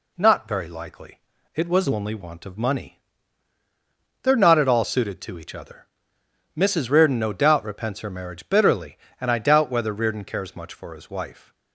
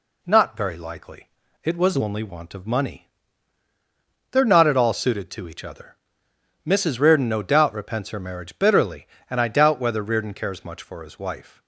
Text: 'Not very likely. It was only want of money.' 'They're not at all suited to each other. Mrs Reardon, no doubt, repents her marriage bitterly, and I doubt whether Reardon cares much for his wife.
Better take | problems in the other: neither | none

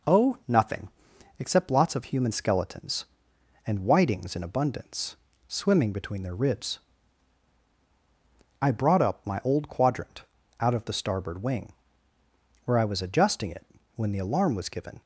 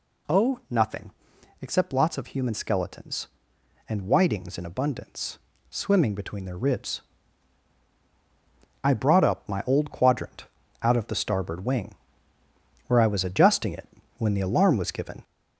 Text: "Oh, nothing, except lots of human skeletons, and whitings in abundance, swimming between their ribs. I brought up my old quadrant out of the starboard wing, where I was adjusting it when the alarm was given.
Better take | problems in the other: first | gets louder; throughout; 4 dB // pauses between "quadrant" and "out"; slight; at 10.4 s; 0.36 s long; slight in the first // pauses between "it" and "when"; slight; at 13.8 s; 0.30 s long; slight in the first

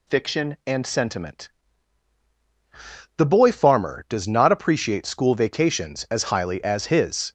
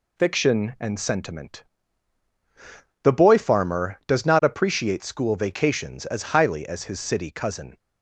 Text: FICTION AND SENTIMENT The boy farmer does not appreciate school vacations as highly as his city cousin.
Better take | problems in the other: second | pauses between "SENTIMENT" and "The"; strong; at 1.4 s; 1.6 s long; strong in the second // stops before "city cousin"; at 7.2 s

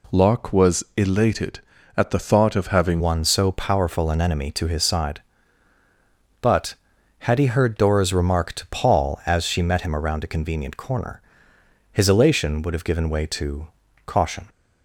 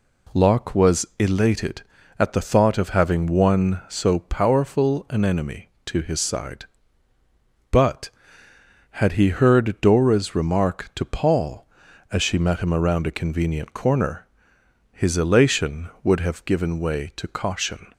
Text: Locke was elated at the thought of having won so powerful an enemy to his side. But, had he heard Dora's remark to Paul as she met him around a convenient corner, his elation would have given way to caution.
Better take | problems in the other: second | changes voice at "won"; from 2.9 s on; 11.5 s long // pauses between "to" and "caution"; at 13.6 s; 0.40 s long

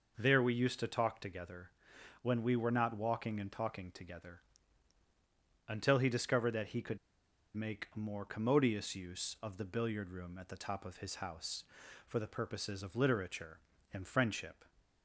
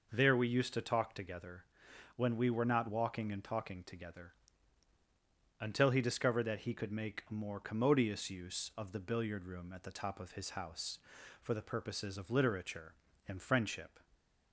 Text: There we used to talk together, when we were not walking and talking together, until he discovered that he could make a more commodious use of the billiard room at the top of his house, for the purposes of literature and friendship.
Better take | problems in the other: second | pauses between "could" and "make"; noticeable; at 6.9 s; 0.58 s long

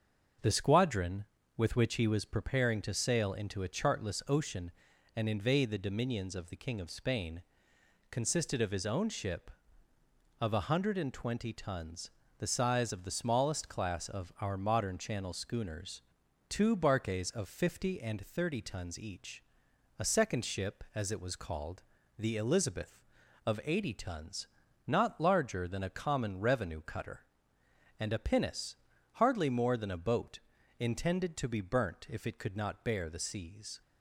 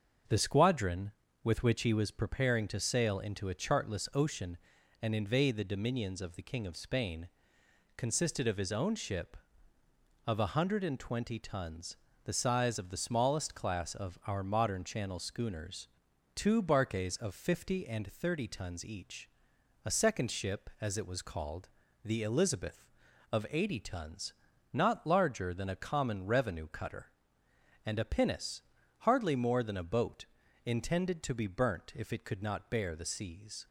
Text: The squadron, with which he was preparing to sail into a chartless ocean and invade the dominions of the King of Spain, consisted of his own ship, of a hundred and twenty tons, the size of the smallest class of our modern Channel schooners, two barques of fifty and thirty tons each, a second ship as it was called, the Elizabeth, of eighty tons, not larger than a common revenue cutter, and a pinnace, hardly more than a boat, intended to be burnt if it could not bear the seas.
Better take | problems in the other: neither | starts louder than the rest; the same in both

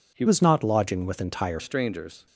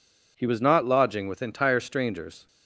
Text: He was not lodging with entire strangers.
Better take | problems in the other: second | changes voice from "was" to "entire"; from 0.2 to 1.6 s; 1.4 s long

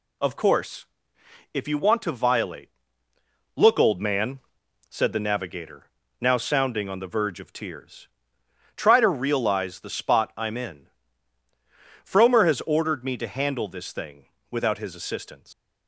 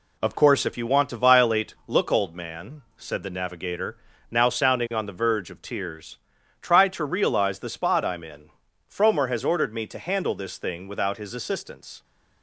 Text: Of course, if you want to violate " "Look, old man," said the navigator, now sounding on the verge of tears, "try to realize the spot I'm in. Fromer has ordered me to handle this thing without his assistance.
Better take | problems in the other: second | pauses between "thing" and "without"; slight; at 14.2 s; 0.24 s long // leaves "assistance" unfinished; at 15.5 s; 125 ms

